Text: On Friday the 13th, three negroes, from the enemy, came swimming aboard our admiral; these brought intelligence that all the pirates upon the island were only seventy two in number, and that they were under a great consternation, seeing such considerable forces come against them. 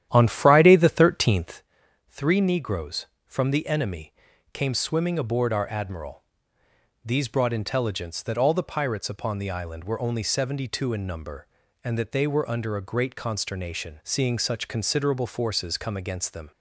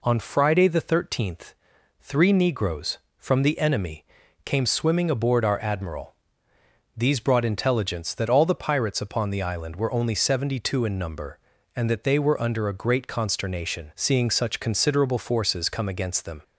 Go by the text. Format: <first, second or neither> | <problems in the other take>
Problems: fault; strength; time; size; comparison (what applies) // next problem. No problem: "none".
second | starts louder than the rest; strong; until 1.6 s; 11 dB